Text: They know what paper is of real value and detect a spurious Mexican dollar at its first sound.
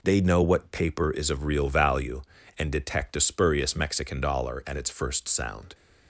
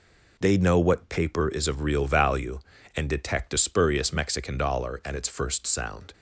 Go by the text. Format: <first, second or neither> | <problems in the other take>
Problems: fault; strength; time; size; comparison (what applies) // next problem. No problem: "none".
neither | none